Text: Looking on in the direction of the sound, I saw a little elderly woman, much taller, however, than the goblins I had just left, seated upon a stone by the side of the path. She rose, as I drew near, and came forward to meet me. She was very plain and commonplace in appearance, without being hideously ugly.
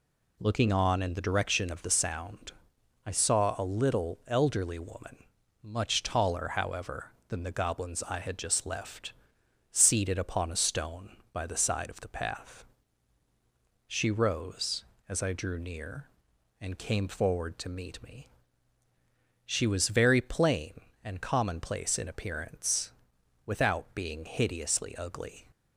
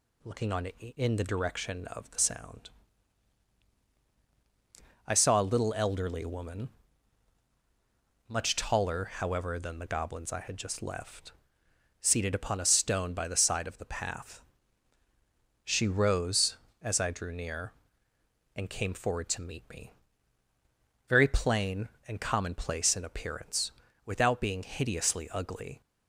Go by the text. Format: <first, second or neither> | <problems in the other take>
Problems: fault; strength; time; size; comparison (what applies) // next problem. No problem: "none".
first | skips "She was"; at 20.5 s